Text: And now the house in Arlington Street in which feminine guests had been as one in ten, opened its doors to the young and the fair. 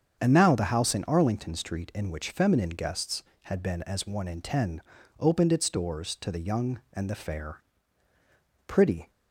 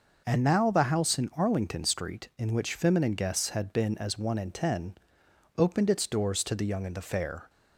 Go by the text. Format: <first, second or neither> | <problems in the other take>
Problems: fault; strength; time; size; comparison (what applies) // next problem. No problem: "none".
second | starts louder than the rest; strong; until 1.2 s; 7.5 dB // goes on to say "Pretty"; slight; from 8.6 s on; 0.44 s long